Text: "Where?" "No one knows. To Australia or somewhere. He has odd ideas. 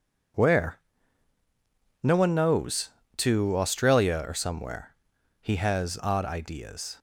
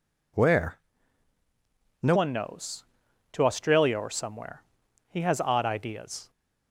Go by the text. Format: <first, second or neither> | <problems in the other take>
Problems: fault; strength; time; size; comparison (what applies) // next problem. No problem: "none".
first | changes voice at "one"; from 2.1 s on; 4.1 s long